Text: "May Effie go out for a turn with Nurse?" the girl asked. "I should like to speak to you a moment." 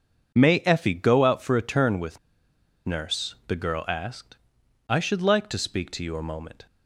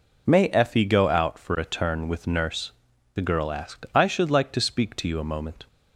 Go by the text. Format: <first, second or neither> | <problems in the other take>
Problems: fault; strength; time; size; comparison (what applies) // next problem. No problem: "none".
second | pauses between "with" and "Nurse"; noticeable; at 2.1 s; 0.67 s long